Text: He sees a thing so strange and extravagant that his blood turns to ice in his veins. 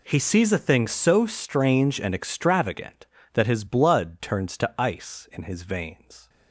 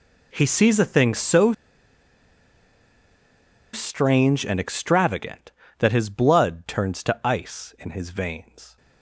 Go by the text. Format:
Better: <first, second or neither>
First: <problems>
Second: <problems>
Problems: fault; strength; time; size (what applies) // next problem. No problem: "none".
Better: first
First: none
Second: pauses between "so" and "strange"; strong; at 1.5 s; 2.2 s long